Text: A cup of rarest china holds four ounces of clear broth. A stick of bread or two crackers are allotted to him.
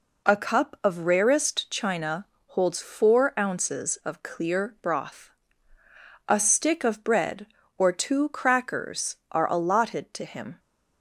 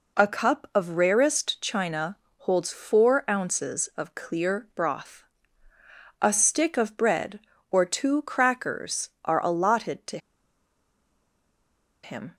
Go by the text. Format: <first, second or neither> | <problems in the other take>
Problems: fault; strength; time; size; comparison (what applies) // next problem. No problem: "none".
first | pauses between "china" and "holds"; slight; at 2.1 s; 0.22 s long; slight in the first // pauses between "to" and "him"; strong; at 10.1 s; 1.8 s long